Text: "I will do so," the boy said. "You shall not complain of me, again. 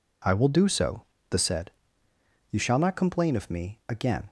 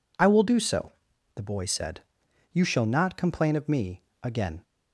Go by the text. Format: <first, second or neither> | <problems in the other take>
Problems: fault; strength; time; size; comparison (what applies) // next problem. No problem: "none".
second | skips "boy"; at 1.3 s